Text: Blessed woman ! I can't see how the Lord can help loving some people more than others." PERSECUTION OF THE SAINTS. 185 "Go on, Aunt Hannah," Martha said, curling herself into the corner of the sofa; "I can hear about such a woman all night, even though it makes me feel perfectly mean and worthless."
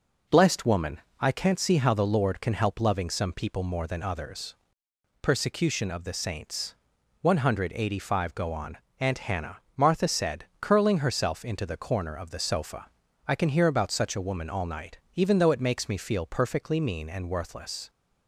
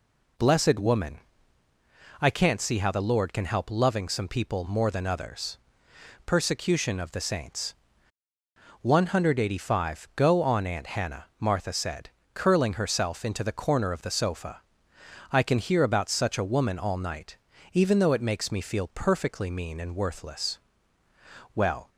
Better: first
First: none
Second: goes on to say "Well"; slight; from 21.5 s on; 0.34 s long

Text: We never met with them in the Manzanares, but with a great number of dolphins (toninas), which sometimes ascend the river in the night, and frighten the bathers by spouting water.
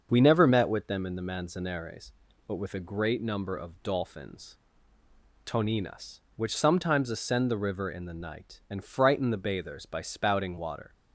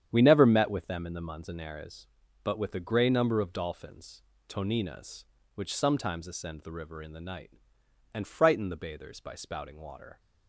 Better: first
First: starts louder than the rest; until 1.1 s; 6.5 dB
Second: starts louder than the rest; strong; until 1.1 s; 9 dB // says "grey" for "great"; at 2.7 s

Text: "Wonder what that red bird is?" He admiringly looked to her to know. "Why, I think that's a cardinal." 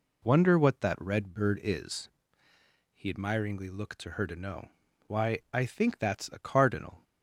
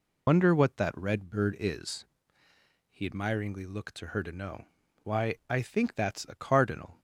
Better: first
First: none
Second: loses the start of "Wonder"; at 0.2 s; 75 ms

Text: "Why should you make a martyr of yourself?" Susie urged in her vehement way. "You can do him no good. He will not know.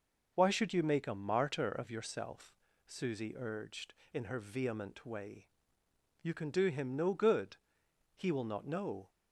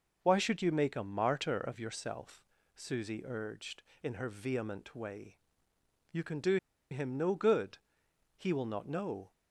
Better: first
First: none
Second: pauses between "do" and "him"; slight; at 6.5 s; 0.34 s long

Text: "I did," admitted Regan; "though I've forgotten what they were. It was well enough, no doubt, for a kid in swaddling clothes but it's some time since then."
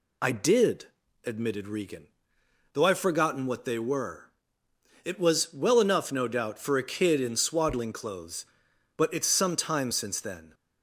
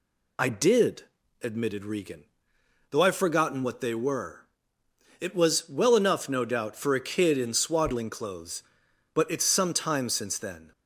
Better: neither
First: none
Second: none

